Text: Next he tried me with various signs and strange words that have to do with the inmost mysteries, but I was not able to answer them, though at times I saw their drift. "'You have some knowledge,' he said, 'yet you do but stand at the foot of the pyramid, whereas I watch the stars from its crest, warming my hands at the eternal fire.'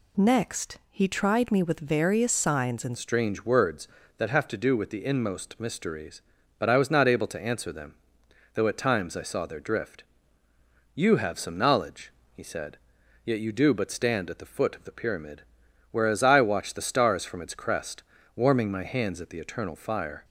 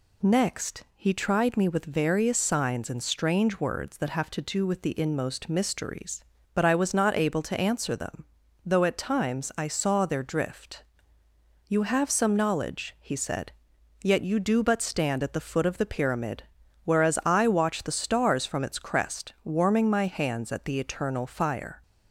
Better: second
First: changes voice at "strange"; from 2.9 s on; 17.3 s long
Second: none

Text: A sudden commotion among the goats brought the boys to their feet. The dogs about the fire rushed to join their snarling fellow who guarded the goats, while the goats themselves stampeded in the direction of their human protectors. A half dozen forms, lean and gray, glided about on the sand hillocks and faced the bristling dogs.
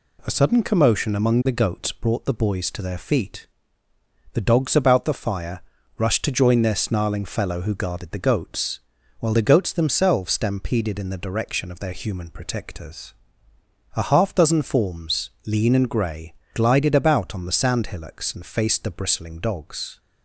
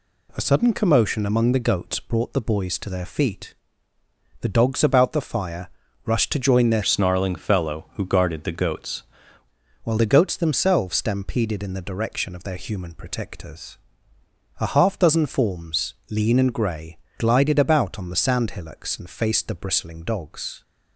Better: first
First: pauses between "fire" and "rushed"; slight; at 5.6 s; 0.36 s long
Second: pauses between "fire" and "rushed"; slight; at 5.6 s; 0.36 s long // changes voice from "snarling" to "goats"; from 6.8 to 9.0 s; 2.2 s long

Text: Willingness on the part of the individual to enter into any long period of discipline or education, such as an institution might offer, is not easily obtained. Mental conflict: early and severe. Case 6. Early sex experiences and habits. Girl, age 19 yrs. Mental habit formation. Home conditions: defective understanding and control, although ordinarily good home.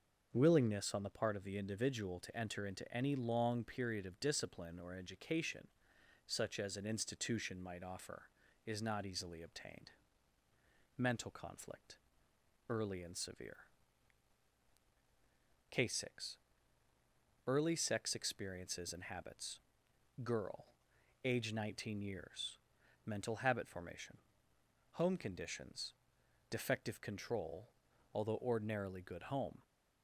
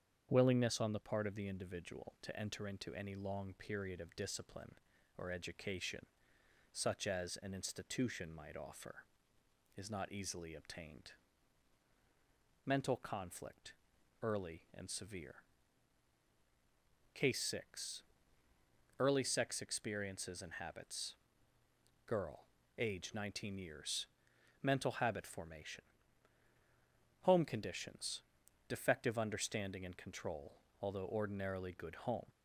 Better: second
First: starts louder than the rest; until 1.3 s; 6.5 dB // skips "understanding and"; at 27.0 s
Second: starts louder than the rest; strong; until 1.3 s; 8 dB

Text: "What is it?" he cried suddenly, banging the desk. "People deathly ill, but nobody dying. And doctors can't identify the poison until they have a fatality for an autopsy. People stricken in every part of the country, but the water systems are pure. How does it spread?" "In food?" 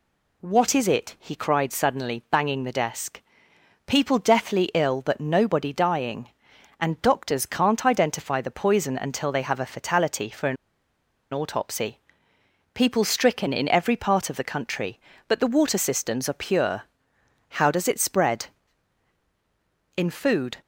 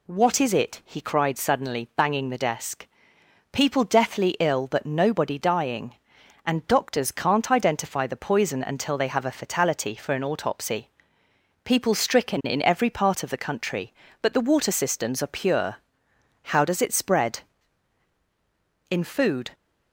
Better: second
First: pauses between "an" and "autopsy"; noticeable; at 10.5 s; 0.76 s long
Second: none

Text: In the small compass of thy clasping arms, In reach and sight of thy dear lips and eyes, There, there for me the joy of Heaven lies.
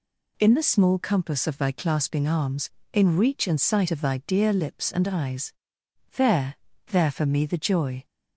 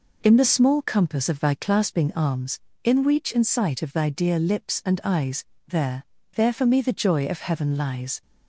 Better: second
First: stops before "of Heaven lies"; at 8.0 s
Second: none

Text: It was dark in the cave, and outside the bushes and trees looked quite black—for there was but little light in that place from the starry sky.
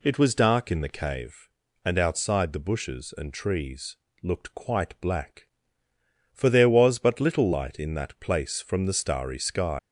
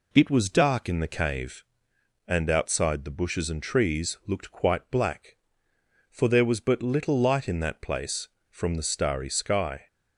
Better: second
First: pauses between "trees" and "looked"; slight; at 3.9 s; 0.26 s long // leaves "sky" unfinished; at 9.7 s; 125 ms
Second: none

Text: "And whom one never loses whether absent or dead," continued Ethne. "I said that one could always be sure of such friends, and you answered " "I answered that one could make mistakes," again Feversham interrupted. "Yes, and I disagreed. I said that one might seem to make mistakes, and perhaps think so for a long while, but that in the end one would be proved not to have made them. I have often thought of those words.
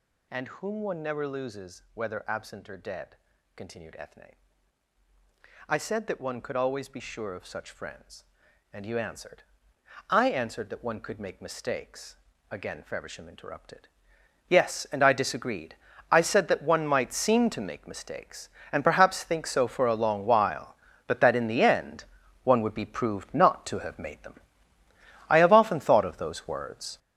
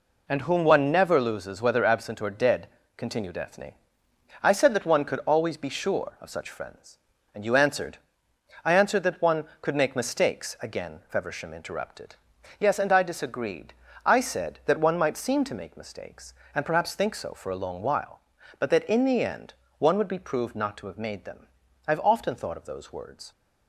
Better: second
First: gets louder; strong; throughout; 9.5 dB // pauses between "end" and "one"; at 22.0 s; 0.40 s long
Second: pauses between "end" and "one"; slight; at 19.5 s; 0.26 s long

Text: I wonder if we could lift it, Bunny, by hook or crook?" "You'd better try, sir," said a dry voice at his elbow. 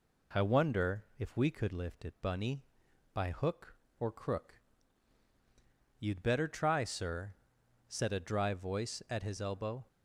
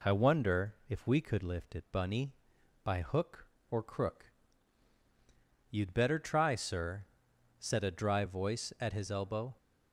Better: neither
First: none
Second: none

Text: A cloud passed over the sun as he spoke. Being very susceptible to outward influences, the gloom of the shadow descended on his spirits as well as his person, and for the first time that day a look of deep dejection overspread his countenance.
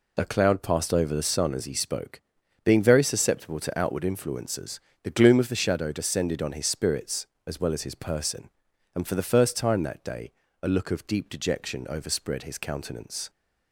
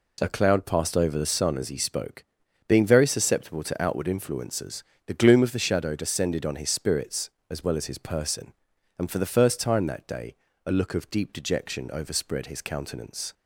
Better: second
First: loses the start of "A"; at 0.1 s; 20 ms // pauses between "day" and "a"; slight; at 10.3 s; 0.30 s long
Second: pauses between "day" and "a"; slight; at 10.3 s; 0.30 s long

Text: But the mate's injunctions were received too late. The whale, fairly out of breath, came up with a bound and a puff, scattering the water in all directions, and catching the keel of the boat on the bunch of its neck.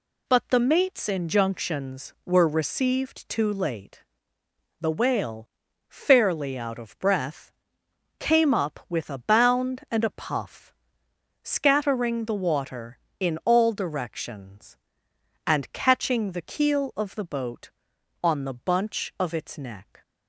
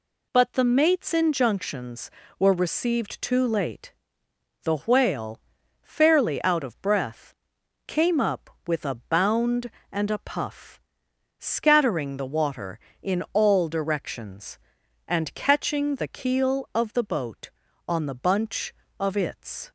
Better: first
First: none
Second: stops before "neck"; at 19.6 s

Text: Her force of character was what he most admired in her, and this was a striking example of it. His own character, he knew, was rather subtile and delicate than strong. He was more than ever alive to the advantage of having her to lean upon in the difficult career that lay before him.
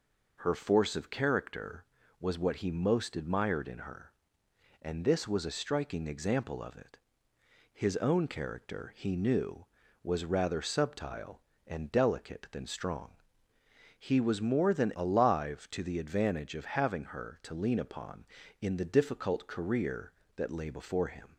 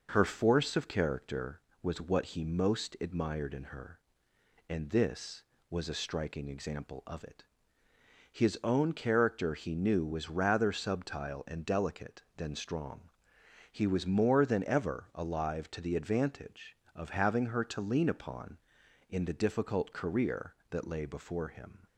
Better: second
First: skips "ever"; at 14.9 s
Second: none

